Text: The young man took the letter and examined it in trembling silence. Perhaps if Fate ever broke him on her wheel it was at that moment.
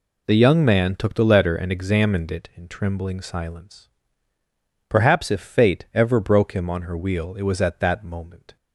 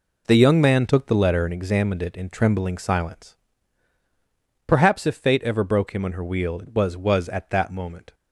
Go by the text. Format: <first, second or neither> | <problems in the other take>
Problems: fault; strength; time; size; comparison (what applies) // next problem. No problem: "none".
first | says "was" twice; at 6.9 s